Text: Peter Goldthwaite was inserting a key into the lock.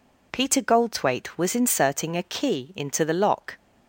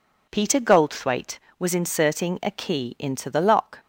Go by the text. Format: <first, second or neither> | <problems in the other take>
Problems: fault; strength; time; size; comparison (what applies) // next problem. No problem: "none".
neither | none